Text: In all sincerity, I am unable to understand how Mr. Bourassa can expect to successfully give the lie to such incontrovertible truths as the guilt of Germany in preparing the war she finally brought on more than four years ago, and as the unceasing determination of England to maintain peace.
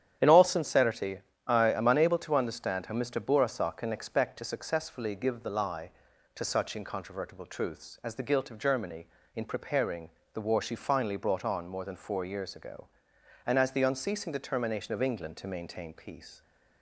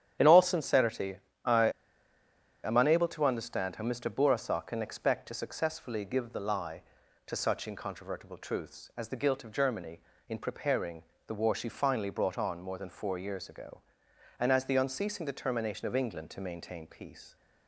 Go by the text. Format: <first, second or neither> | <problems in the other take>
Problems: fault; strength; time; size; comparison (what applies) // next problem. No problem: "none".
first | starts louder than the rest; strong; until 1.4 s; 9.5 dB; strong in the first // pauses between "I" and "am"; noticeable; at 1.6 s; 0.94 s long // pauses between "preparing" and "the"; slight; at 11.0 s; 0.24 s long; slight in the first